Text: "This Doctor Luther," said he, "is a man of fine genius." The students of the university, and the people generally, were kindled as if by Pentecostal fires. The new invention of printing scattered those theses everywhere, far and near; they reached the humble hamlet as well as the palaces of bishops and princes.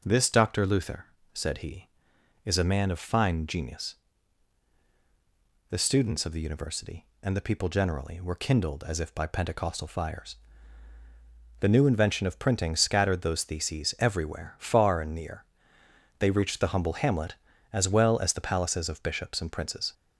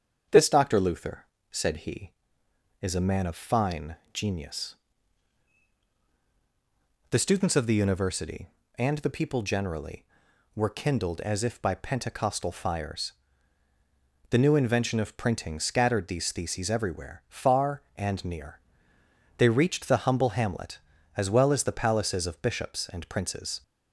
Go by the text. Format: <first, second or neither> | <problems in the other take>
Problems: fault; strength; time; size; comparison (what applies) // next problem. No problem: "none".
first | starts louder than the rest; strong; until 1.5 s; 7.5 dB // pauses between "fine" and "genius"; slight; at 3.9 s; 0.16 s long // says "these" for "those"; at 16.0 s